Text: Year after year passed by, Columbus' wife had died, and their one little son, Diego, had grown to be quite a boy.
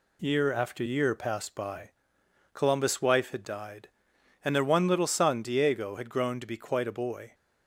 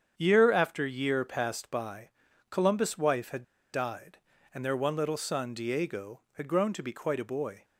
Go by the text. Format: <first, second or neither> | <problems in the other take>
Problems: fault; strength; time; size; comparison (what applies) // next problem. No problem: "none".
first | starts louder than the rest; strong; until 1.1 s; 8 dB // pauses between "had" and "died"; slight; at 3.4 s; 0.30 s long